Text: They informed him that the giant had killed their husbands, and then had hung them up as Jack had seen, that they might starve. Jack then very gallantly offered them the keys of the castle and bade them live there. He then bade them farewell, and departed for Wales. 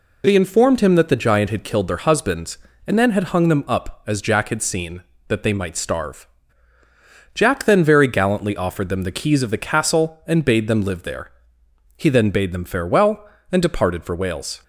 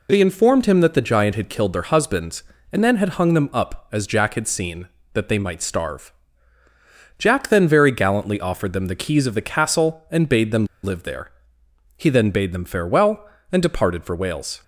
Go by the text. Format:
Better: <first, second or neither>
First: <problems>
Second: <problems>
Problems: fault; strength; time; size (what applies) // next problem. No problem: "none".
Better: first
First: none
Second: pauses between "them" and "live"; slight; at 10.6 s; 0.18 s long